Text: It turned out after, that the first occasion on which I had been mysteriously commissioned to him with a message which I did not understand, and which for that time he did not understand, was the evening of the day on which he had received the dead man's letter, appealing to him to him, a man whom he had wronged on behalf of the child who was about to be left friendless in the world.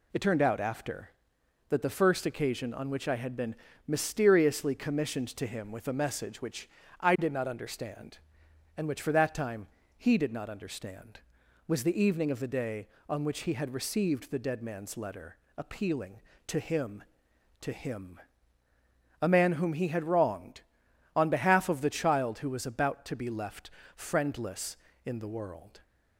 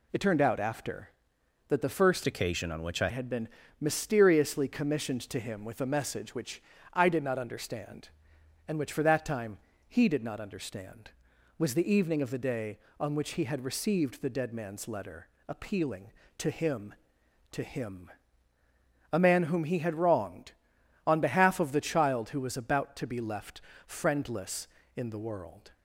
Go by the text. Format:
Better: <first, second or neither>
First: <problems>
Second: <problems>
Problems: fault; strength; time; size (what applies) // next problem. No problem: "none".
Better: first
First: pauses between "been" and "mysteriously"; slight; at 3.5 s; 0.32 s long // pauses between "which" and "I"; slight; at 6.6 s; 0.30 s long // pauses between "time" and "he"; slight; at 9.6 s; 0.30 s long // pauses between "left" and "friendless"; slight; at 23.7 s; 0.24 s long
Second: changes voice from "occasion" to "I"; from 2.2 to 3.0 s; 0.8 s long // pauses between "been" and "mysteriously"; slight; at 3.4 s; 0.32 s long // pauses between "which" and "I"; slight; at 6.6 s; 0.30 s long // pauses between "time" and "he"; slight; at 9.5 s; 0.30 s long // pauses between "left" and "friendless"; slight; at 23.6 s; 0.24 s long